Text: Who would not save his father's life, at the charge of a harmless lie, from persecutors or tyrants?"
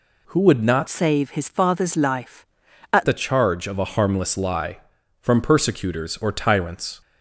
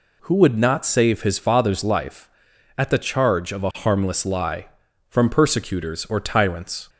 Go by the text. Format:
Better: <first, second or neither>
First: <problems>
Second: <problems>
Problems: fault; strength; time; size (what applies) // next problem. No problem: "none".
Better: second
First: changes voice from "save" to "at"; from 0.8 to 3.0 s; 2.2 s long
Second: none